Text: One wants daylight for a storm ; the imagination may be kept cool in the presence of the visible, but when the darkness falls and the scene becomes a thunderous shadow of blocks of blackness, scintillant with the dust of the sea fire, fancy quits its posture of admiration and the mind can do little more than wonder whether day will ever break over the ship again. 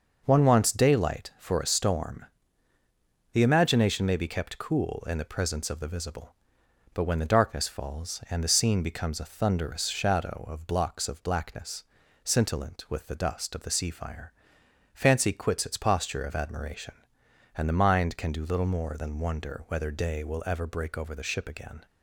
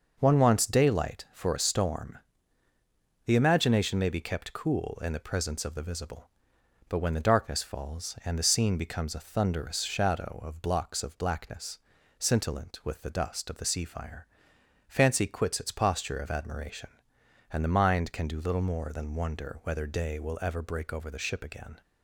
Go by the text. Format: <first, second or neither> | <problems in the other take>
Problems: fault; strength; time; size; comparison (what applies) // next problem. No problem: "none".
neither | none